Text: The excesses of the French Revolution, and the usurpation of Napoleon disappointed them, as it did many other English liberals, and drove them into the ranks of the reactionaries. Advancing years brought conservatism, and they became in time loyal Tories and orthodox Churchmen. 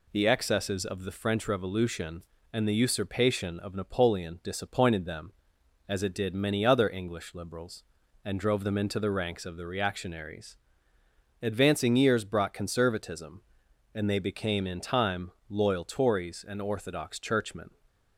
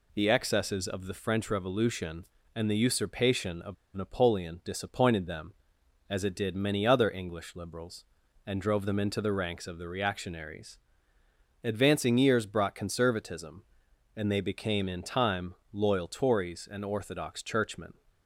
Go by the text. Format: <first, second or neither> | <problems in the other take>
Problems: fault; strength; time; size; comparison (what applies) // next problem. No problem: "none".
first | pauses between "of" and "Napoleon"; slight; at 3.7 s; 0.20 s long // pauses between "time" and "loyal"; slight; at 15.5 s; 0.16 s long; slight in the first